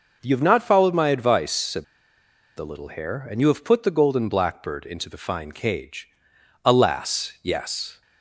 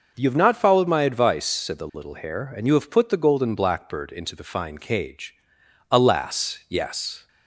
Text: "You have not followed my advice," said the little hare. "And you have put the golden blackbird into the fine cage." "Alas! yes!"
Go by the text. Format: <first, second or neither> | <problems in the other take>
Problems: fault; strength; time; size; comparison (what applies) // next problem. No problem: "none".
second | pauses between "said" and "the"; noticeable; at 1.8 s; 0.72 s long